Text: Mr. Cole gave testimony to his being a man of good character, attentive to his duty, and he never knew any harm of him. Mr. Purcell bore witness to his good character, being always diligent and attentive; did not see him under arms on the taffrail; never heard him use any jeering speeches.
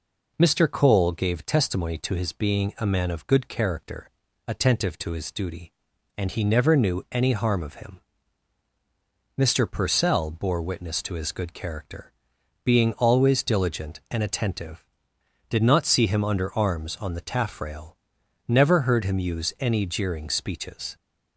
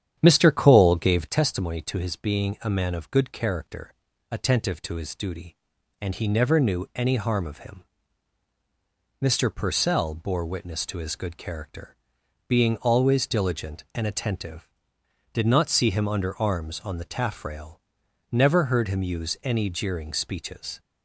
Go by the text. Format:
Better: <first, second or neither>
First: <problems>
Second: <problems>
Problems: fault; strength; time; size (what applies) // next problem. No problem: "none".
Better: first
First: none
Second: starts louder than the rest; strong; until 1.4 s; 9.5 dB